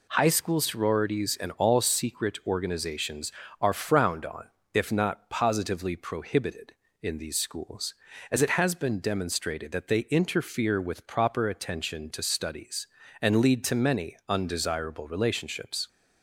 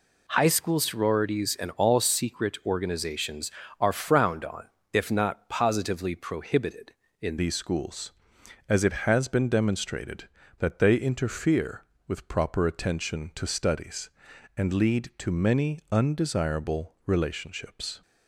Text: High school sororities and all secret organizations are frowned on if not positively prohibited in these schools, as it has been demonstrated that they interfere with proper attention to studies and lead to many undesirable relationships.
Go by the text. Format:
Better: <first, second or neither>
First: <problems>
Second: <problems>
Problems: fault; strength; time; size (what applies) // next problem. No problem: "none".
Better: first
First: pauses between "on" and "if"; slight; at 4.4 s; 0.26 s long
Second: pauses between "on" and "if"; slight; at 4.6 s; 0.26 s long // changes voice at "these"; from 7.3 s on; 10.7 s long